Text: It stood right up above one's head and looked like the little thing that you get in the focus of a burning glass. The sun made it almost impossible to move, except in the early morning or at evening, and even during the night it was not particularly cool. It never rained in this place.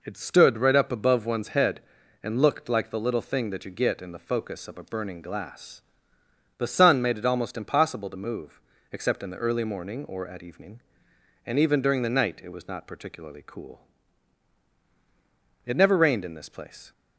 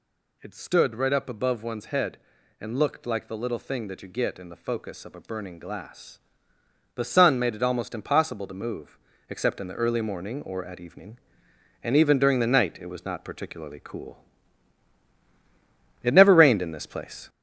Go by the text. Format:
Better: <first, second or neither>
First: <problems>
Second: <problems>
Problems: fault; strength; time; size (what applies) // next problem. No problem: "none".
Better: first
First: none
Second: gets louder; noticeable; throughout; 4.5 dB